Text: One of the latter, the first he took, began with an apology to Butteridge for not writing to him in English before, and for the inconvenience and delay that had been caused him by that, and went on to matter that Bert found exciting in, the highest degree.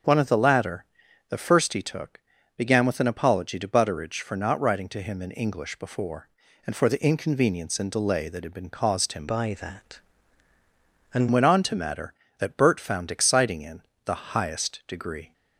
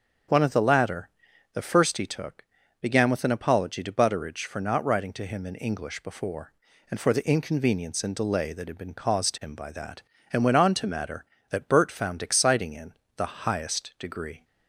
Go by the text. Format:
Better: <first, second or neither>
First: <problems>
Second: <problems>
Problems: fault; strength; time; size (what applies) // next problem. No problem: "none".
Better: second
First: starts louder than the rest; until 1.5 s; 6.5 dB // changes voice from "by" to "and"; from 9.2 to 11.2 s; 2.0 s long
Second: starts louder than the rest; until 1.7 s; 6.5 dB